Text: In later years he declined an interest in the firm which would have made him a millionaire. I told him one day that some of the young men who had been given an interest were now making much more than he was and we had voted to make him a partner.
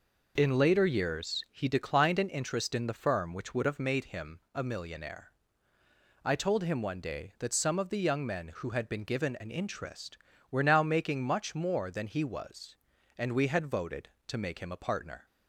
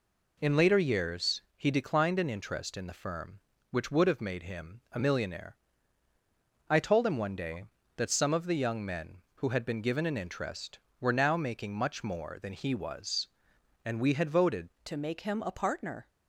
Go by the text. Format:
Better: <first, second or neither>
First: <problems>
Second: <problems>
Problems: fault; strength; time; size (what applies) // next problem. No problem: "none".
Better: first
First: none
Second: changes voice at "to"; from 14.8 s on; 1.2 s long